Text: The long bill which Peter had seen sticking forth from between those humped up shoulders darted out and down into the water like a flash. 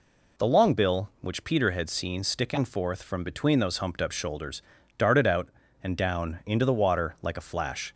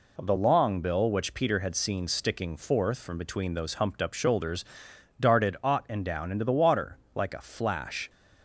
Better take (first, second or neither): first